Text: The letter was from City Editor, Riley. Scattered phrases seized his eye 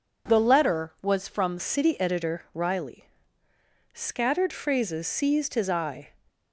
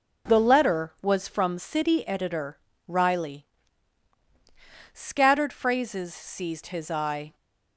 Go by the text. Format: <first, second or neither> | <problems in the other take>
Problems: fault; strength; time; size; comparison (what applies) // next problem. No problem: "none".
second | changes voice at "City"; from 1.5 s on; 4.6 s long